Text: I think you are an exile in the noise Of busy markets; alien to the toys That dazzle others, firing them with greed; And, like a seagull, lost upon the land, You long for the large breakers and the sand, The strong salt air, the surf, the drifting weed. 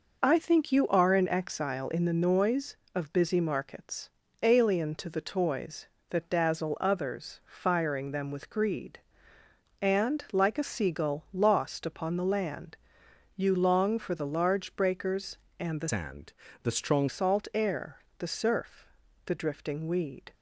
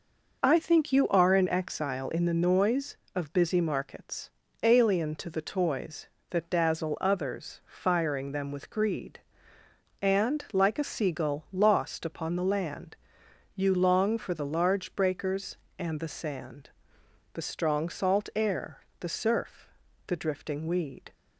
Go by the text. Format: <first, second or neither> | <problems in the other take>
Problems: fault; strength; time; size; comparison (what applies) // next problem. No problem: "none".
second | changes voice from "sand" to "strong"; from 15.8 to 17.0 s; 1.2 s long